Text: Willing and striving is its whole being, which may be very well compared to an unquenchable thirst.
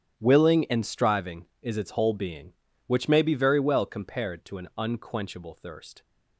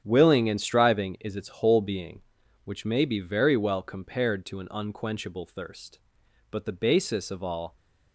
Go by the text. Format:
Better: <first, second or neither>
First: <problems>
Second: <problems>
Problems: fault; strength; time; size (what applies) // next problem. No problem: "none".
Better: first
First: starts louder than the rest; strong; until 1.2 s; 10 dB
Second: starts louder than the rest; strong; until 1.0 s; 9 dB // goes on to say "But the basis of all"; noticeable; from 6.4 s on; 1.2 s long